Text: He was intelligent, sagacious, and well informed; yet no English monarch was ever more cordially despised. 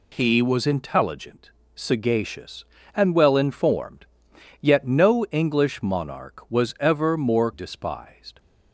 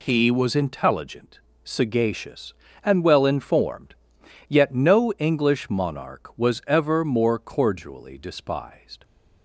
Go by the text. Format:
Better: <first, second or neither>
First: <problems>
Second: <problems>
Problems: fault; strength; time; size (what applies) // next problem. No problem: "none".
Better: second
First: skips "cordially"; at 7.5 s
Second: none